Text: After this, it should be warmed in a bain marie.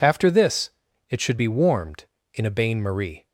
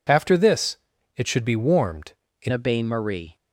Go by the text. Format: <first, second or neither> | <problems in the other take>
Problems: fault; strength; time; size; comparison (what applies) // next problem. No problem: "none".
first | changes voice at "a"; from 2.5 s on; 0.8 s long